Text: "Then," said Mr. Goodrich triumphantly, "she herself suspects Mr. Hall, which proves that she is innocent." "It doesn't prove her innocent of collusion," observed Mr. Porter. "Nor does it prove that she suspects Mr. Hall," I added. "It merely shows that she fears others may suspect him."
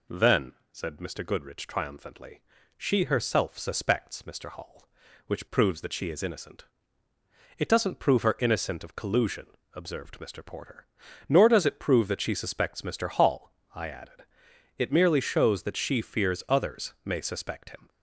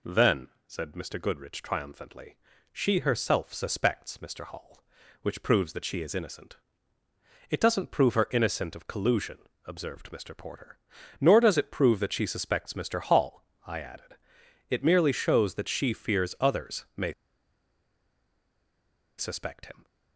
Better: first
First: none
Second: pauses between "may" and "suspect"; strong; at 17.1 s; 2.0 s long

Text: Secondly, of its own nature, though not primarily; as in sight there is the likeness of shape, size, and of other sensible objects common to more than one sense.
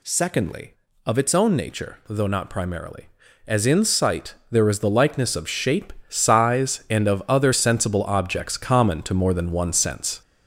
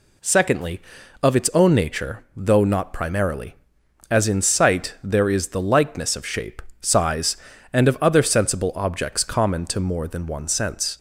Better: second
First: gets louder; noticeable; throughout; 4.5 dB // pauses between "sight" and "there"; slight; at 4.3 s; 0.16 s long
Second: none

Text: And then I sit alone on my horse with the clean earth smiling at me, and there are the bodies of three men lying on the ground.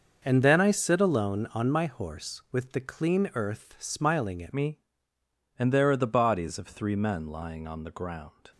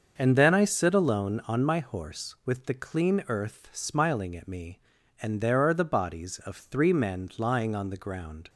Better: second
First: starts louder than the rest; until 1.2 s; 6.5 dB // changes voice at "me"; from 4.5 s on; 3.9 s long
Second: starts louder than the rest; until 1.1 s; 6.5 dB

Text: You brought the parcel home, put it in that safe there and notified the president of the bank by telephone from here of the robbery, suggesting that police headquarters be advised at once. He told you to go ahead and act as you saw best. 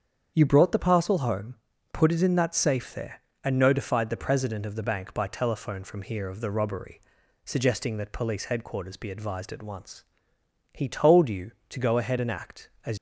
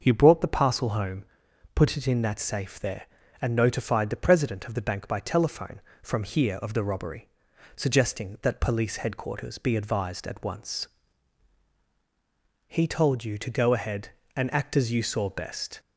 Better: second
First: starts louder than the rest; strong; until 1.3 s; 7.5 dB // stops before "you saw best"; at 12.9 s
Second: starts louder than the rest; until 1.0 s; 6.5 dB

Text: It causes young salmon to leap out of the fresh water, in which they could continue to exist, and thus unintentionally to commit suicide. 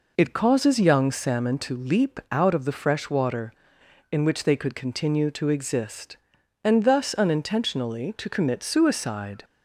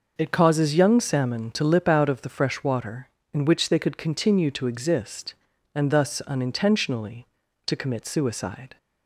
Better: first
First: none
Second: says "lip" for "leap"; at 1.6 s

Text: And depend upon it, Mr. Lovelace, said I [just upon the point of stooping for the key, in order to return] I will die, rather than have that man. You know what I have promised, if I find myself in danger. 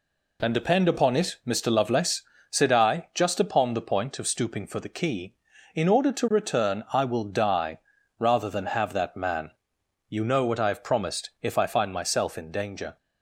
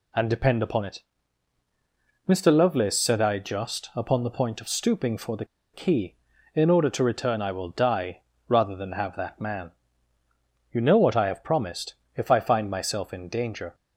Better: first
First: none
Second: pauses between "the" and "key"; slight; at 5.4 s; 0.29 s long

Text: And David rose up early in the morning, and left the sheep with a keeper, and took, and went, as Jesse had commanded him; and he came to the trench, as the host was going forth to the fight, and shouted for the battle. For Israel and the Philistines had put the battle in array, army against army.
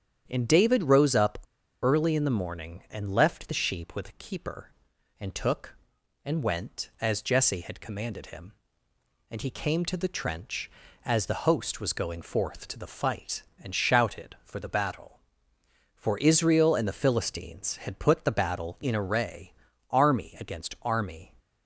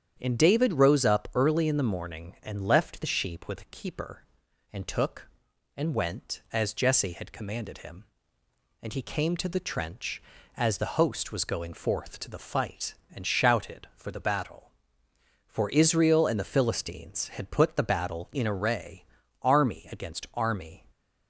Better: second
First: starts louder than the rest; strong; until 1.2 s; 8.5 dB // pauses between "up" and "early"; at 1.3 s; 0.44 s long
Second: starts louder than the rest; strong; until 1.2 s; 8.5 dB

